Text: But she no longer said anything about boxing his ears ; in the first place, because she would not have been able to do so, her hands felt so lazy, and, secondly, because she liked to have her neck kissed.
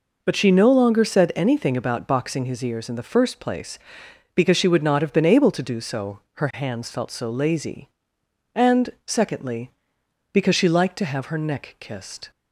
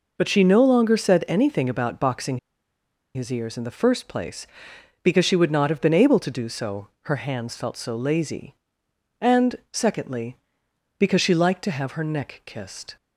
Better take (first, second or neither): first